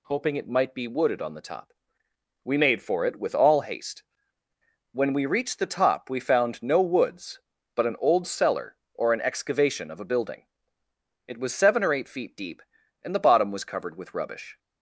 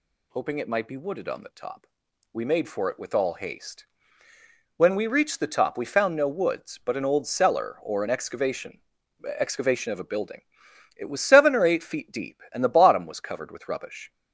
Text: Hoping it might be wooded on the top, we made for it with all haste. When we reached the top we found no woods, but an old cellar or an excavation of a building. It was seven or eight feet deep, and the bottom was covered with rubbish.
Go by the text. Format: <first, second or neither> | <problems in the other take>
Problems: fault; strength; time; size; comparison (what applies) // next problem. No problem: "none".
first | says "excavation" twice; at 9.3 s